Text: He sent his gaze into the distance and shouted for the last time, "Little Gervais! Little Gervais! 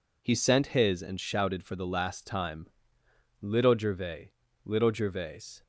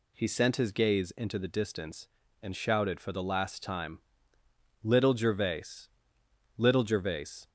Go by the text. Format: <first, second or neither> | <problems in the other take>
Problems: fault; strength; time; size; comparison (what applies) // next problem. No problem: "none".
second | skips "gaze into the distance"; at 1.0 s